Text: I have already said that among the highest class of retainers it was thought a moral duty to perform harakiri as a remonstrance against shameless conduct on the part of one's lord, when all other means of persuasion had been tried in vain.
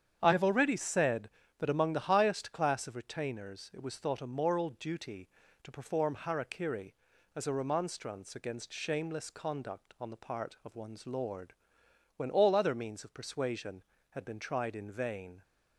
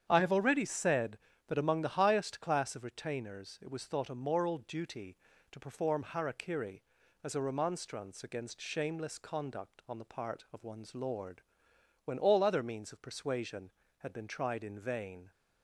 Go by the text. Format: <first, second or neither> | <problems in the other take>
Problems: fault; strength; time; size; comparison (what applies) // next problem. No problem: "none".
neither | starts louder than the rest; strong; the same in both